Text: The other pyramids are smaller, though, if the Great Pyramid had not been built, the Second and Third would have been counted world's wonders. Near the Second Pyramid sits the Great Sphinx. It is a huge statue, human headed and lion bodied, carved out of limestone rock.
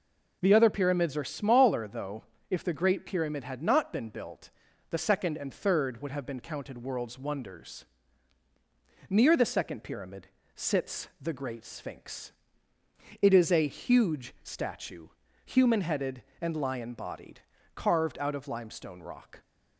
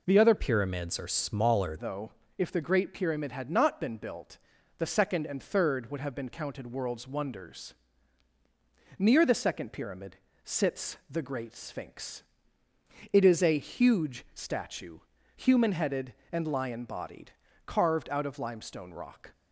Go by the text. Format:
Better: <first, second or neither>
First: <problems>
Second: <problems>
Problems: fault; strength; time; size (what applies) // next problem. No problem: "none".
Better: first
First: pauses between "Pyramid" and "sits"; slight; at 10.2 s; 0.26 s long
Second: changes voice from "pyramids" to "smaller"; from 0.3 to 1.7 s; 1.4 s long // pauses between "Pyramid" and "sits"; slight; at 10.1 s; 0.26 s long